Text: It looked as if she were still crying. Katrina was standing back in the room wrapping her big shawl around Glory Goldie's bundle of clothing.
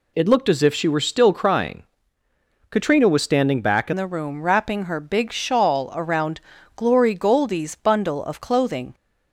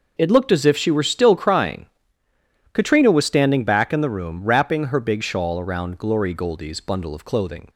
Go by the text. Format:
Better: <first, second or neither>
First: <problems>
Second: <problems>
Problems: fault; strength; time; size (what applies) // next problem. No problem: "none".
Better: second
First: changes voice at "the"; from 3.9 s on; 5.0 s long // pauses between "around" and "Glory"; slight; at 6.4 s; 0.34 s long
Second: none